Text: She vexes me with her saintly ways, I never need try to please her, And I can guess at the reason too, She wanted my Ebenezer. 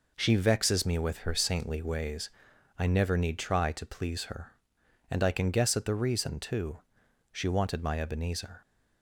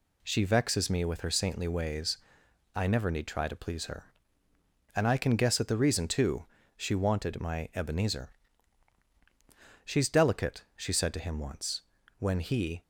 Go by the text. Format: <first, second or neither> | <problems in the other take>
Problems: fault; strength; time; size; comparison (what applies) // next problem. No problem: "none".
first | goes on to say "She's delicate she said to him once When he"; strong; from 9.8 s on; 2.9 s long